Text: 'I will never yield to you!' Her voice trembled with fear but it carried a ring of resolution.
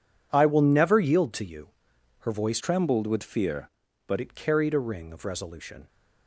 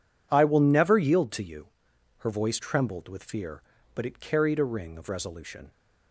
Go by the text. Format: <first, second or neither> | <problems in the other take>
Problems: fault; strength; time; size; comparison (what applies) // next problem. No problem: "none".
second | changes voice from "trembled" to "but"; from 2.6 to 4.1 s; 1.5 s long